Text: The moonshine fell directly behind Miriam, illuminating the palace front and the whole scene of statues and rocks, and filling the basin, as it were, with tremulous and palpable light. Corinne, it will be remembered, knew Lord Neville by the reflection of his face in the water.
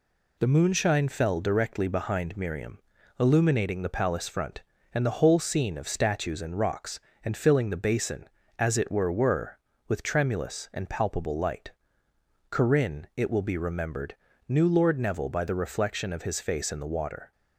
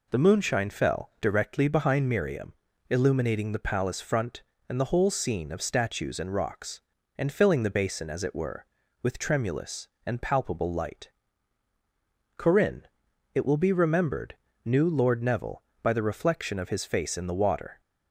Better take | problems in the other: second | says "were" twice; at 9.1 s

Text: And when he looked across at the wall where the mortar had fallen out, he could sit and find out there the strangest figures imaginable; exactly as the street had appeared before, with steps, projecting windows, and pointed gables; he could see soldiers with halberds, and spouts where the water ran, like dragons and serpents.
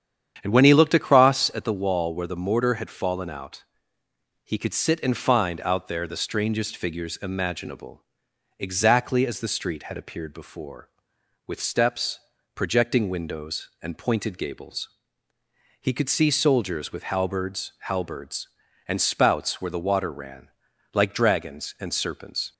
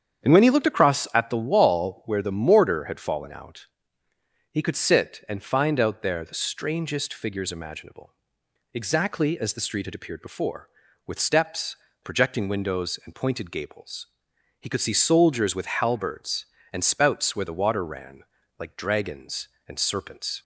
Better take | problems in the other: second | starts louder than the rest; strong; until 1.4 s; 8.5 dB; strong in the second // says "halberds" twice; at 17.8 s

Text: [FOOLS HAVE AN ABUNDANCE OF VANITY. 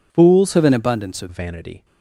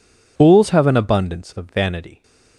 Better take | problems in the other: second | changes voice from "HAVE" to "OF"; from 0.5 to 1.2 s; 0.7 s long

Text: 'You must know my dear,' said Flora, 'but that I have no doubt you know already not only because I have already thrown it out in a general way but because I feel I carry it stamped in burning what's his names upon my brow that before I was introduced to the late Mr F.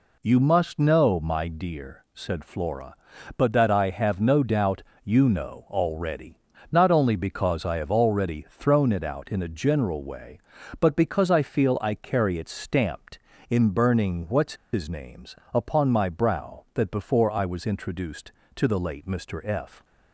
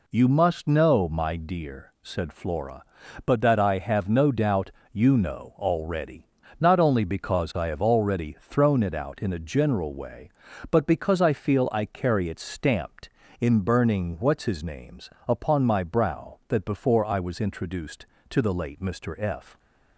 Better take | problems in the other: second | pauses between "doubt" and "you"; slight; at 4.8 s; 0.22 s long; slight in the second // pauses between "already" and "not"; slight; at 6.3 s; 0.34 s long; slight in the second // pauses between "what's" and "his"; slight; at 14.5 s; 0.19 s long // pauses between "names" and "upon"; slight; at 15.3 s; 0.20 s long; slight in the second

